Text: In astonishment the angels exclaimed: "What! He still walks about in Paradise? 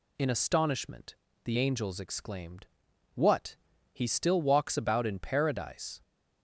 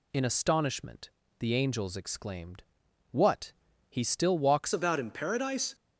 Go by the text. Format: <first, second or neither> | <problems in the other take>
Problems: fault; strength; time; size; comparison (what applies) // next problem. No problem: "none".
first | pauses between "astonishment" and "the"; slight; at 1.1 s; 0.28 s long; slight in the first // changes voice at "about"; from 4.7 s on; 1.0 s long